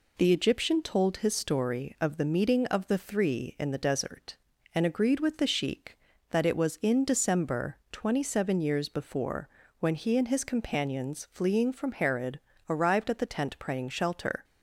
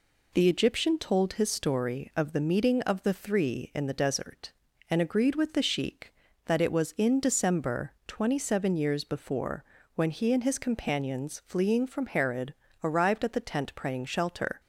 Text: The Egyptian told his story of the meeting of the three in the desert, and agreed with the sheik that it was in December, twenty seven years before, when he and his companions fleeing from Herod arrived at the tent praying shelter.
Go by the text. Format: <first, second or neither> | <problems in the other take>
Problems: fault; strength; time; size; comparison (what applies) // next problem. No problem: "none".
neither | pauses between "Herod" and "arrived"; slight; the same in both